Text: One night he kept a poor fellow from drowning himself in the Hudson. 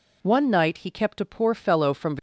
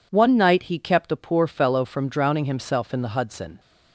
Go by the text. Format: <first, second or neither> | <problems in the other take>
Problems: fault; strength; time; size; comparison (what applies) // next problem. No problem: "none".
second | stops before "drowning himself in the Hudson"; at 2.1 s